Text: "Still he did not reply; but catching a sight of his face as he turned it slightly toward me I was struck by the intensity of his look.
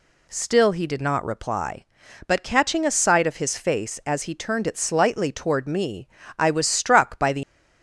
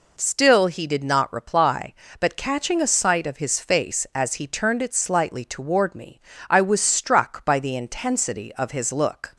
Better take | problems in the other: second | pauses between "me" and "I"; slight; at 6.0 s; 0.32 s long; slight in the second // stops before "intensity of his look"; at 7.4 s

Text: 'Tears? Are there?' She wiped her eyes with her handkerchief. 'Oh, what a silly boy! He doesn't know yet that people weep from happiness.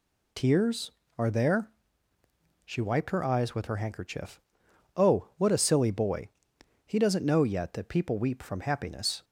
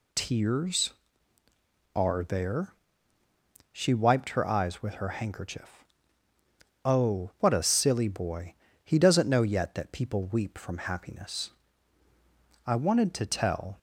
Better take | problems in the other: first | goes on to say "I wanted to tell"; noticeable; from 12.6 s on; 1.1 s long

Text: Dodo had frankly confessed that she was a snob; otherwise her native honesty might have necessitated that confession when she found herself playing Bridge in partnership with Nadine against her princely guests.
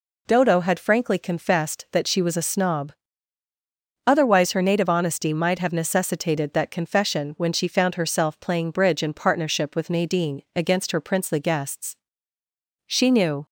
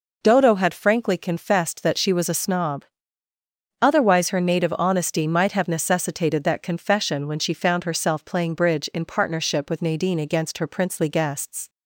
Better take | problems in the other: second | goes on to say "She knew"; from 12.8 s on; 0.58 s long

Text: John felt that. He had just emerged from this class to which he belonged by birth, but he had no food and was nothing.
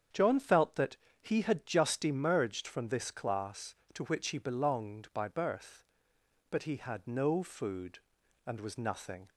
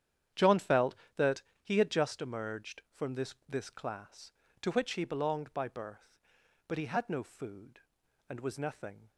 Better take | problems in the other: first | starts louder than the rest; strong; until 1.7 s; 9.5 dB; strong in the first // says "this" twice; at 3.4 s

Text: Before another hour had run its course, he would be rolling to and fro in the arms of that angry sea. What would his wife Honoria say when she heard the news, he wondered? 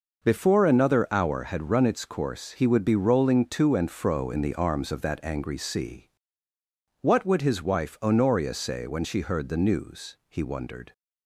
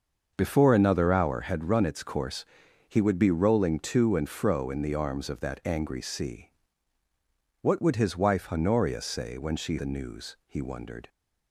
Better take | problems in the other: first | starts louder than the rest; until 1.3 s; 6.5 dB // skips "heard"; at 9.7 s

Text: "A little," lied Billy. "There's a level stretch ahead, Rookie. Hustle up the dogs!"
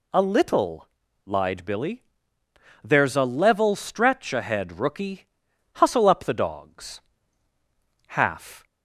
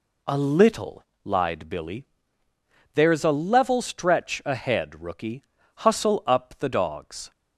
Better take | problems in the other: second | goes on to say "Half"; from 8.0 s on; 0.58 s long

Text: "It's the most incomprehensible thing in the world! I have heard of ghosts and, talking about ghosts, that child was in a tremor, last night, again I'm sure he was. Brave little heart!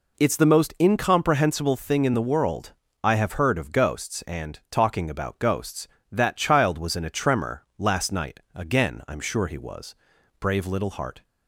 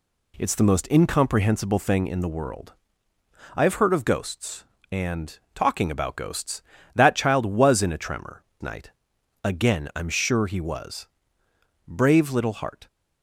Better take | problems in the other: first | skips "last"; at 8.5 s

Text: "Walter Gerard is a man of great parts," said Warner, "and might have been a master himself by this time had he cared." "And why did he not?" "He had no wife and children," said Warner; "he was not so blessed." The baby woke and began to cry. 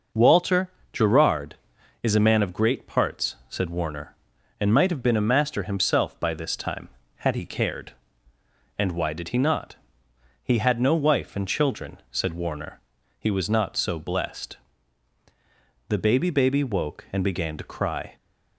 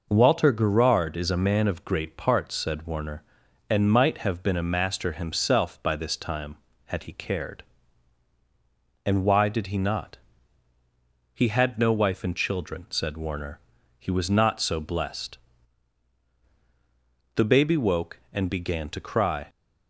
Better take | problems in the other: second | pauses between "Walter" and "Gerard"; slight; at 0.7 s; 0.20 s long // says "baby" twice; at 16.3 s

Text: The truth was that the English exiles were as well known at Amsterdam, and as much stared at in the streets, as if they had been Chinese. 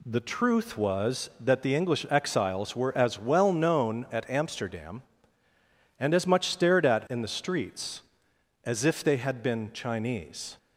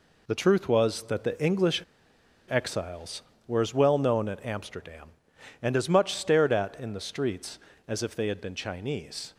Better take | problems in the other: first | pauses between "English" and "exiles"; noticeable; at 1.8 s; 0.67 s long

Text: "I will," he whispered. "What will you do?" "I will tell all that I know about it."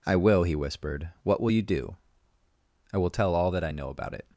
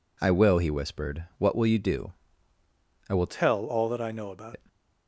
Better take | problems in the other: first | changes voice from "tell" to "about"; from 3.2 to 4.5 s; 1.3 s long

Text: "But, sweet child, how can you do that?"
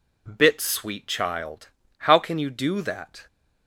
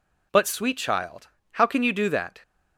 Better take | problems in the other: second | says "Bit" for "But"; at 0.2 s

